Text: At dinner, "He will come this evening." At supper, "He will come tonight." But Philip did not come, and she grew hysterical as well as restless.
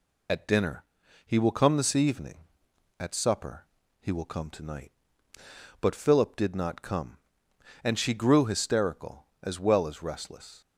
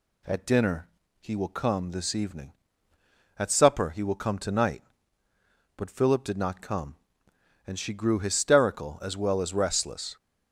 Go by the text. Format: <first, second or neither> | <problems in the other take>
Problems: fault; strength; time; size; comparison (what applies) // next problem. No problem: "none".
second | loses the start of "At"; at 0.2 s; 50 ms